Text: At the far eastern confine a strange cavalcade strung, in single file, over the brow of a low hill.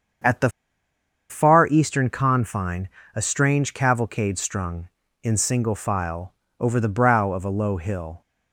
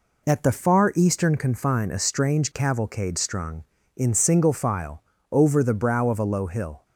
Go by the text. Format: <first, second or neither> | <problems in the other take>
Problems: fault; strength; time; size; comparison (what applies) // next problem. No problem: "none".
second | starts louder than the rest; strong; until 2.0 s; 7 dB // pauses between "the" and "far"; noticeable; at 0.4 s; 0.81 s long // pauses between "confine" and "a"; slight; at 2.8 s; 0.28 s long